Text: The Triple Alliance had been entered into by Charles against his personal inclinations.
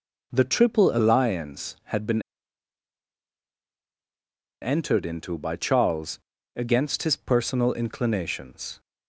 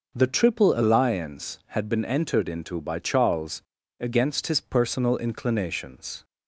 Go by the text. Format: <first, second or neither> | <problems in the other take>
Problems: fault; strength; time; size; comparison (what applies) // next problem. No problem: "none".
second | pauses between "been" and "entered"; strong; at 2.2 s; 2.4 s long // pauses between "Charles" and "against"; at 6.1 s; 0.38 s long; also in the second